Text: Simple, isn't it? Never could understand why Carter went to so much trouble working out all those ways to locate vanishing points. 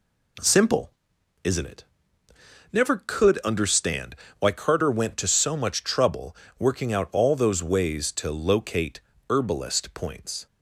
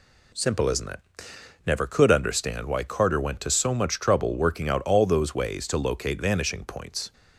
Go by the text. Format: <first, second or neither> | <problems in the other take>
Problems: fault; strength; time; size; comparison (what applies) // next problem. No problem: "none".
second | pauses between "understand" and "why"; slight; at 4.1 s; 0.24 s long // pauses between "trouble" and "working"; slight; at 6.3 s; 0.22 s long // says "herbalist" for "vanishing"; at 9.2 s